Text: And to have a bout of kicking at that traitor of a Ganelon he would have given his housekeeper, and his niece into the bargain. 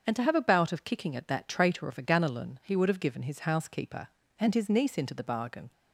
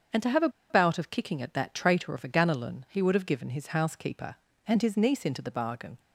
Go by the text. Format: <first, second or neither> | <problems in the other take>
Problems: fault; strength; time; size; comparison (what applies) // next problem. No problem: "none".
first | starts louder than the rest; until 1.3 s; 7 dB; also in the first // pauses between "a" and "bout"; slight; at 0.4 s; 0.21 s long